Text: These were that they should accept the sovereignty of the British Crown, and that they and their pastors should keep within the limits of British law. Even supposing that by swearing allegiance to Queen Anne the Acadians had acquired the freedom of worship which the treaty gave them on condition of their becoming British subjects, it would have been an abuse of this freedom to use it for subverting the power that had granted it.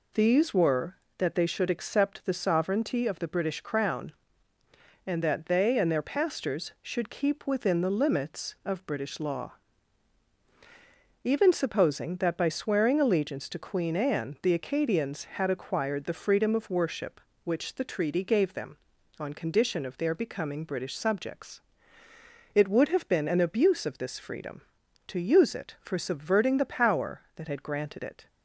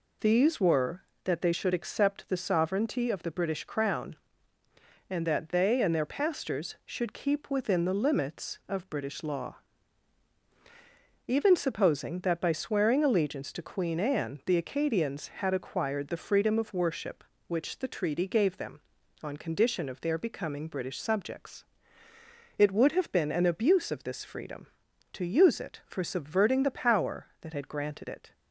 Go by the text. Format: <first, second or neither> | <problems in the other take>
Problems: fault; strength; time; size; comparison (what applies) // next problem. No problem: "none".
neither | none